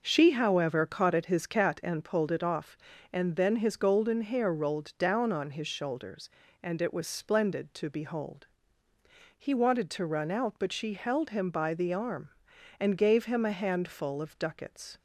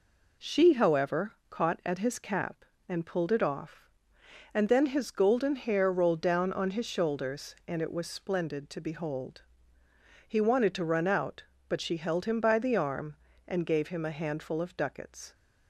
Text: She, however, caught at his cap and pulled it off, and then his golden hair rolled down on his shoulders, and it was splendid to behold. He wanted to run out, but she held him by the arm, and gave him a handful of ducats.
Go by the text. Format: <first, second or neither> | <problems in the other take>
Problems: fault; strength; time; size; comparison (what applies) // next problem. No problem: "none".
second | says "cat" for "cap"; at 1.4 s